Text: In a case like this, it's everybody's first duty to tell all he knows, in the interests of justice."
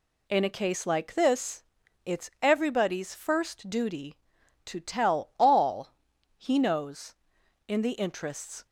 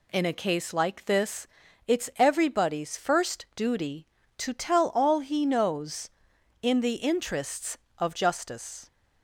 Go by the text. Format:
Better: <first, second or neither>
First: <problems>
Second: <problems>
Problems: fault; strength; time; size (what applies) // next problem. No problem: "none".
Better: second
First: pauses between "all" and "he"; noticeable; at 5.8 s; 0.46 s long // stops before "of justice"; at 8.6 s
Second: none